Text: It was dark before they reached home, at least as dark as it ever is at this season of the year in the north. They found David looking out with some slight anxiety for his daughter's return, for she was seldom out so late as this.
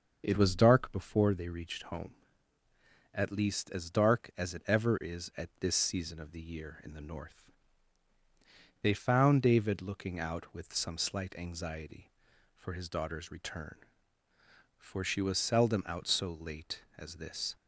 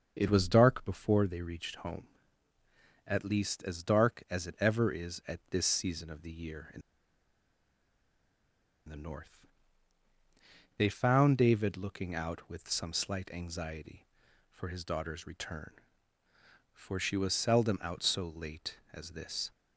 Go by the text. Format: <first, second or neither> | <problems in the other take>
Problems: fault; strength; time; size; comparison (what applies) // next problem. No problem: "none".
first | starts louder than the rest; until 1.1 s; 6.5 dB; also in the first // pauses between "in" and "the"; strong; at 6.8 s; 2.0 s long